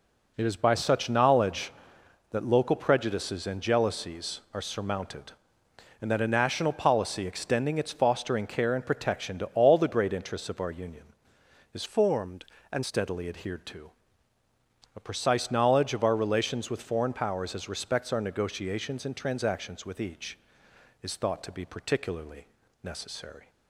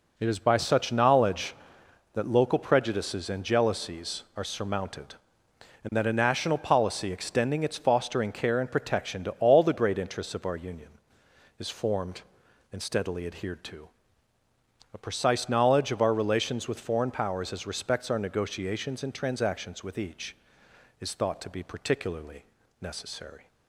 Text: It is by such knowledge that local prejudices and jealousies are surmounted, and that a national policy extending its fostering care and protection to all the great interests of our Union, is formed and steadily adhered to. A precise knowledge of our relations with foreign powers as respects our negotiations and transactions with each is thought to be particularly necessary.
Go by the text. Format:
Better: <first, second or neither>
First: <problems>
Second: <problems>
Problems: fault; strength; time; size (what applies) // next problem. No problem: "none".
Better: second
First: changes voice from "formed" to "and"; from 11.8 to 12.8 s; 1.0 s long // pauses between "particularly" and "necessary"; slight; at 22.4 s; 0.36 s long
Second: pauses between "particularly" and "necessary"; slight; at 22.4 s; 0.36 s long